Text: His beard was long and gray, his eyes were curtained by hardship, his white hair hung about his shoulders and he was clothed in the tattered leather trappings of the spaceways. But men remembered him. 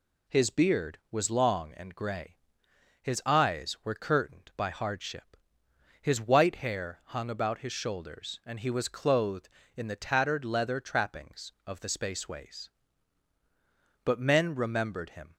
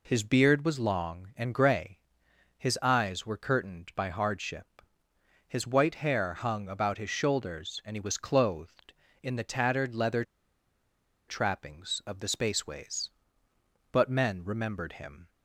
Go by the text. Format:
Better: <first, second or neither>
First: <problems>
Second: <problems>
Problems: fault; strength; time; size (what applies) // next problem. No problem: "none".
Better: first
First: none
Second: pauses between "leather" and "trappings"; at 10.2 s; 1.0 s long